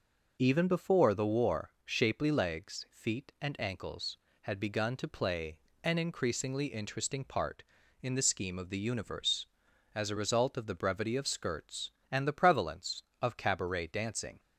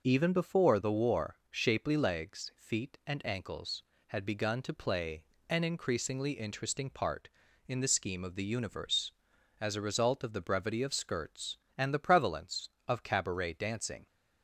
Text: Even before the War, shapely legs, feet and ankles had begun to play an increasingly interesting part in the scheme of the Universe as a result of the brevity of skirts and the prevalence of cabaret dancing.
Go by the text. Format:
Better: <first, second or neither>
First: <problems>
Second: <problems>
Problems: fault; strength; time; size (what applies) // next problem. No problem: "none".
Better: neither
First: pauses between "play" and "an"; slight; at 5.5 s; 0.26 s long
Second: pauses between "play" and "an"; slight; at 5.2 s; 0.26 s long